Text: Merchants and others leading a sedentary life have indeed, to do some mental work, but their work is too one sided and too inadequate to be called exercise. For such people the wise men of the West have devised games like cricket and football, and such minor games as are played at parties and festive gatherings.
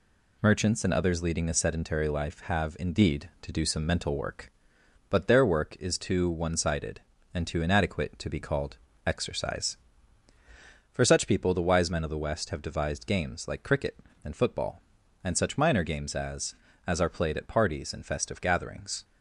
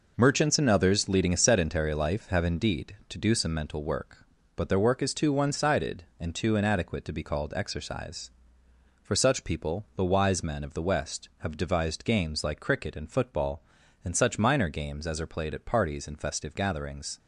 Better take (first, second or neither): second